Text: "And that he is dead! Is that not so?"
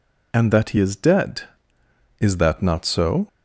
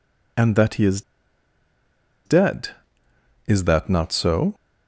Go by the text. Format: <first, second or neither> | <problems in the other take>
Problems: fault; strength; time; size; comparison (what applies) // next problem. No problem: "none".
first | pauses between "is" and "dead"; strong; at 1.0 s; 1.2 s long